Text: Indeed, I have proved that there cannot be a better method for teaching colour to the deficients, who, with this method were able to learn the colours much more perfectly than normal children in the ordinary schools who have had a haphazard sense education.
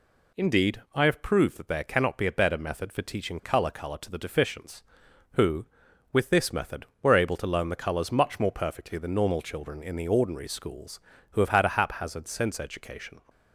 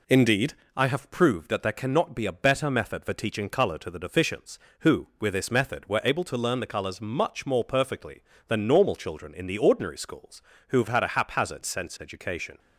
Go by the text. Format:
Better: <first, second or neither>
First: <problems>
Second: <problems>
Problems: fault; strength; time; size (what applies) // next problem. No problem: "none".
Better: second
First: says "colour" twice; at 3.6 s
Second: none